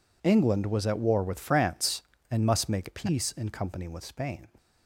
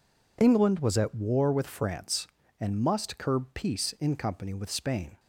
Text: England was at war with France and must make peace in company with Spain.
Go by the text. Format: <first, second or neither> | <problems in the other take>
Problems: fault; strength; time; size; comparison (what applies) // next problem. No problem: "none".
first | says "curb" for "make"; at 3.1 s